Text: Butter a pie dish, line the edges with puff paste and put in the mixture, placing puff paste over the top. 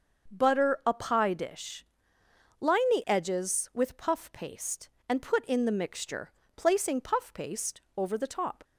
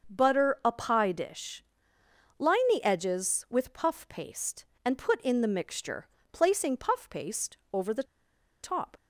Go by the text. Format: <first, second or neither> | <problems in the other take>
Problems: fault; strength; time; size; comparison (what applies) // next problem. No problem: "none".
first | starts louder than the rest; until 1.1 s; 6.5 dB; also in the first // pauses between "paste" and "over"; slight; at 7.5 s; 0.16 s long; slight in the first // pauses between "the" and "top"; noticeable; at 8.0 s; 0.59 s long